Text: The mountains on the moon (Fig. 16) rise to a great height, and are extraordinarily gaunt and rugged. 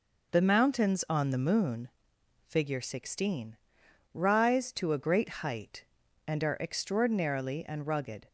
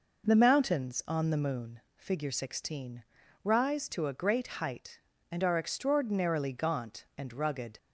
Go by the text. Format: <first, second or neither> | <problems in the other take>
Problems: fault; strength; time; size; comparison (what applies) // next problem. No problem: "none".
second | skips "gaunt"; at 7.6 s